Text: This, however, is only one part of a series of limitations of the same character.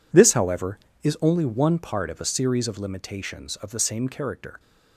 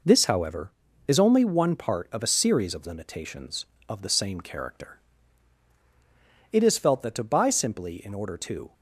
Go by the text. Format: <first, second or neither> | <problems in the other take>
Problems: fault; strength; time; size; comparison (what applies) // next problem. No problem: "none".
first | goes on to say "It is felt that to buy simply in order to"; strong; from 6.5 s on; 2.2 s long